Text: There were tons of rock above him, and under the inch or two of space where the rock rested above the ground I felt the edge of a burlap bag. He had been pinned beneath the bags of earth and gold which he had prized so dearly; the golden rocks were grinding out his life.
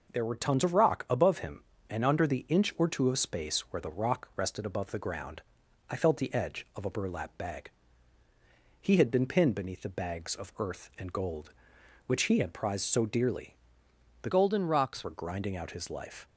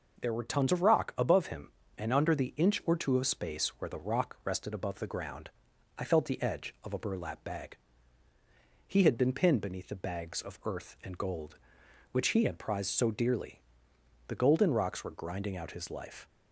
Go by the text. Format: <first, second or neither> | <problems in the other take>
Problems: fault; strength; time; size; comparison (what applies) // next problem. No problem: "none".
second | pauses between "ground" and "I"; noticeable; at 5.4 s; 0.48 s long; noticeable in the second // changes voice from "golden" to "rocks"; from 14.2 to 15.0 s; 0.8 s long